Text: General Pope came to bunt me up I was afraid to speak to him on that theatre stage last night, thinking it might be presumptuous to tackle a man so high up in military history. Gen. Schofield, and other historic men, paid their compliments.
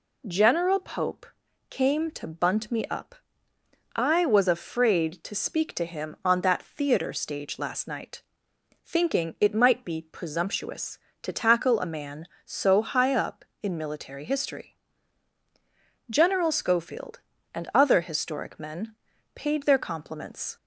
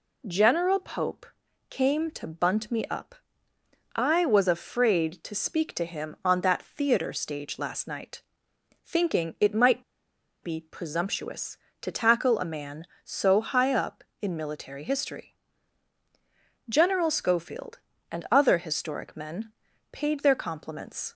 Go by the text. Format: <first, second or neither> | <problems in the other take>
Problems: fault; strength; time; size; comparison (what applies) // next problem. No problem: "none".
first | pauses between "Pope" and "came"; at 1.2 s; 0.42 s long; also in the first // pauses between "up" and "I"; noticeable; at 3.1 s; 0.80 s long; noticeable in the first // pauses between "might" and "be"; noticeable; at 9.8 s; 0.59 s long